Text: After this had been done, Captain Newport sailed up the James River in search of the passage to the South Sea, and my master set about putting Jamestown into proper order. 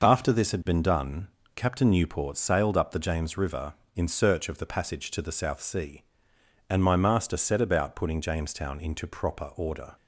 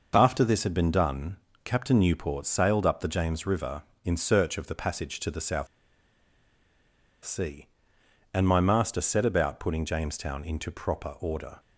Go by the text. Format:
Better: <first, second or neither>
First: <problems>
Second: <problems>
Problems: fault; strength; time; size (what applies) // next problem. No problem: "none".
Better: first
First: none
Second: pauses between "South" and "Sea"; strong; at 5.6 s; 1.5 s long